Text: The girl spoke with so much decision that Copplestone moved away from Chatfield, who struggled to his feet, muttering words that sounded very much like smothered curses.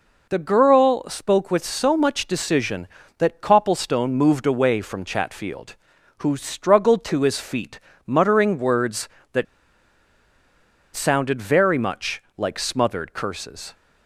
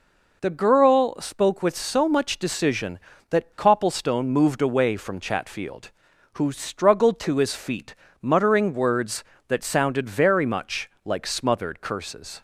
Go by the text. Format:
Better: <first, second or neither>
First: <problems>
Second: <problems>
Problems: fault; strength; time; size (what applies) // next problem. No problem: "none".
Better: second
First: pauses between "that" and "sounded"; strong; at 9.4 s; 1.4 s long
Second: none